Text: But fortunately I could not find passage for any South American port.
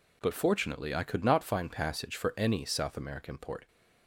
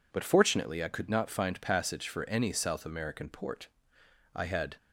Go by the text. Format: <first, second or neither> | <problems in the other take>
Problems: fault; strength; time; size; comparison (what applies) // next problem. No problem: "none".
first | goes on to say "I had"; slight; from 4.3 s on; 0.42 s long